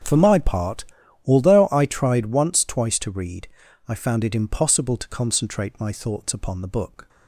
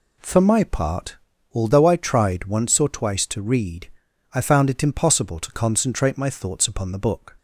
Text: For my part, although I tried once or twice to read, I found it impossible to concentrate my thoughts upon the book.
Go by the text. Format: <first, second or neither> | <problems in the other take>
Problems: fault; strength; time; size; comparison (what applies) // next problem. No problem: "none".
second | starts louder than the rest; until 1.4 s; 7 dB // skips "or"; at 2.6 s